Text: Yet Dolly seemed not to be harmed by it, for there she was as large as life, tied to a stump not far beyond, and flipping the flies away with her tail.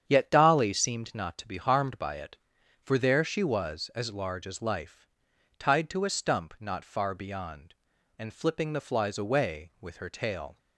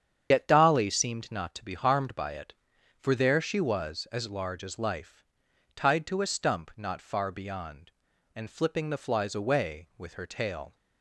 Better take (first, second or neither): first